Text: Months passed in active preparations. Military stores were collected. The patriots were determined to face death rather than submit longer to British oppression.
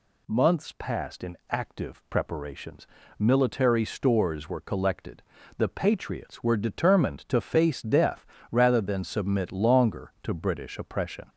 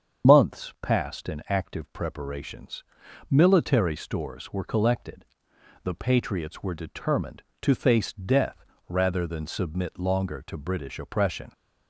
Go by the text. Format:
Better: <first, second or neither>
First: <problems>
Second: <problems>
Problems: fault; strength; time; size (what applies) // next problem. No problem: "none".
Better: first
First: pauses between "death" and "rather"; slight; at 8.2 s; 0.26 s long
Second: loses the start of "Months"; at 0.2 s; 70 ms // starts louder than the rest; strong; until 1.3 s; 7.5 dB // pauses between "death" and "rather"; slight; at 8.6 s; 0.24 s long